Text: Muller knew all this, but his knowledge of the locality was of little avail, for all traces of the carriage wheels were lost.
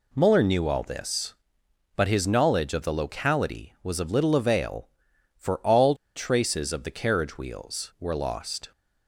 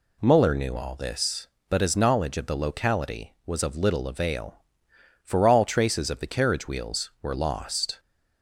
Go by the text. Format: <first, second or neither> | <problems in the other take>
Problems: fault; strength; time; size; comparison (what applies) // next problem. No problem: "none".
second | pauses between "all" and "traces"; slight; at 5.9 s; 0.21 s long